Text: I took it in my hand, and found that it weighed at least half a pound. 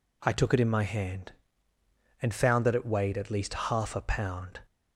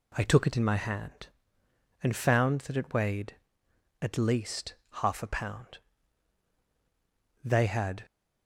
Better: first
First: none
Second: pauses between "least" and "half"; slight; at 4.7 s; 0.26 s long // goes on to say "They had"; noticeable; from 7.4 s on; 0.62 s long

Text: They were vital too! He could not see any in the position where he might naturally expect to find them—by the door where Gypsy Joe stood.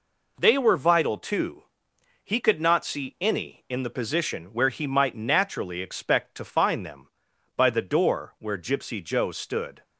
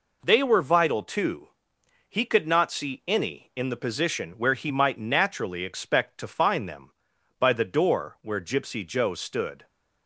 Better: neither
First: none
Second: none

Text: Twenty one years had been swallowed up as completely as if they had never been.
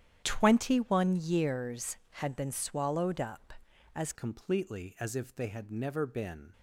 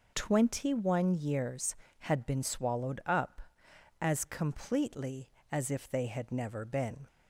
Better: second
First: starts louder than the rest; strong; until 1.2 s; 10 dB // changes voice at "completely"; from 4.1 s on; 2.4 s long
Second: none

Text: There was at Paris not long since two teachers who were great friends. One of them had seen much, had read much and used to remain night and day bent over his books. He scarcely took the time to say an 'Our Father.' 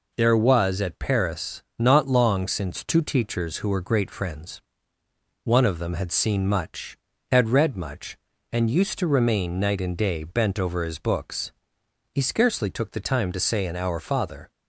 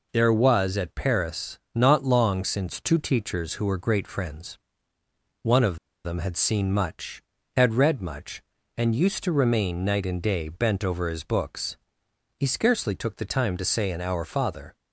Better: first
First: pauses between "Paris" and "not"; slight; at 1.6 s; 0.16 s long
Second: pauses between "Paris" and "not"; slight; at 1.5 s; 0.16 s long // pauses between "of" and "them"; slight; at 5.7 s; 0.27 s long

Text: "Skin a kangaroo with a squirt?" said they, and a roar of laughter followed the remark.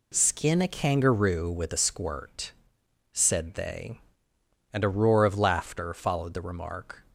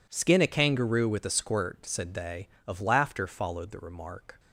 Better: first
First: none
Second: skips "and a roar"; at 2.5 s

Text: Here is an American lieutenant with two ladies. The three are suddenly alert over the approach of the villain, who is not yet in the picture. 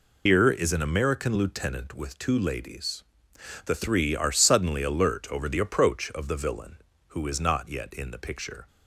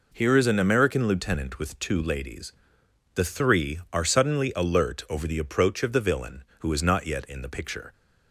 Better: second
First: loses the start of "Here"; at 0.2 s; 90 ms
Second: none

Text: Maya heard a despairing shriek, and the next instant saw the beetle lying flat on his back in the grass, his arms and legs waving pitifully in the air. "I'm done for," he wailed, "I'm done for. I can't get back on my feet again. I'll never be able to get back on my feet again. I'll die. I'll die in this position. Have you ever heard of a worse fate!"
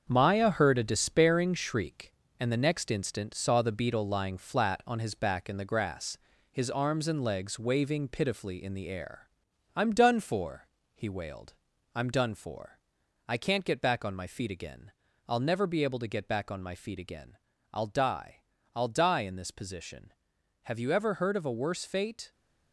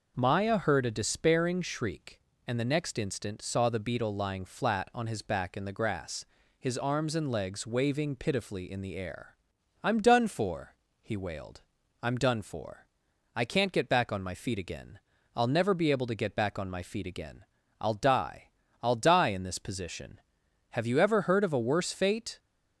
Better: second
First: gets quieter; strong; throughout; 7.5 dB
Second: none

